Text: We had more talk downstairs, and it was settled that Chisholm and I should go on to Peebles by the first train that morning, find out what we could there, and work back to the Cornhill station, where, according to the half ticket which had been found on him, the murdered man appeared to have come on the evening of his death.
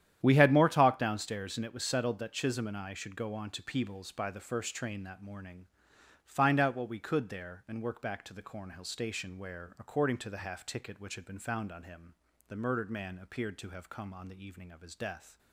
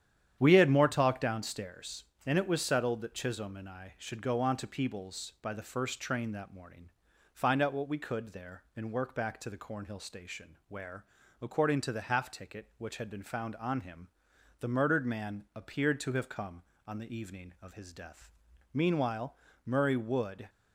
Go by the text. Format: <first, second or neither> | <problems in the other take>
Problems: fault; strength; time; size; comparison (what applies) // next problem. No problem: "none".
first | starts louder than the rest; strong; until 1.4 s; 9.5 dB; strong in the first // goes on to say "Meanwhile Murray would"; strong; from 18.7 s on; 1.7 s long